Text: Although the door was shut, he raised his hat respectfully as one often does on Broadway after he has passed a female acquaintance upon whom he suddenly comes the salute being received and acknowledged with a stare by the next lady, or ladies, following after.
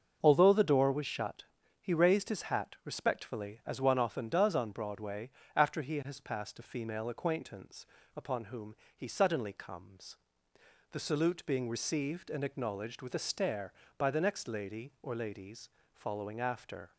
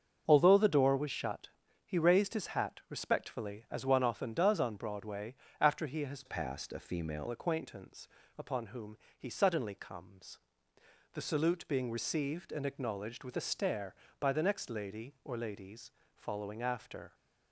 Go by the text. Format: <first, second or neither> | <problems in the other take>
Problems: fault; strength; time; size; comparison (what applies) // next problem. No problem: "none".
first | starts louder than the rest; until 1.2 s; 6.5 dB; also in the first // pauses between "Broadway" and "after"; slight; at 5.3 s; 0.26 s long; slight in the first // changes voice from "passed" to "female"; from 6.2 to 7.2 s; 1.0 s long // pauses between "acquaintance" and "upon"; slight; at 8.0 s; 0.30 s long; slight in the first // pauses between "whom" and "he"; slight; at 8.9 s; 0.20 s long; slight in the first // pauses between "comes" and "the"; noticeable; at 10.3 s; 0.76 s long; noticeable in the first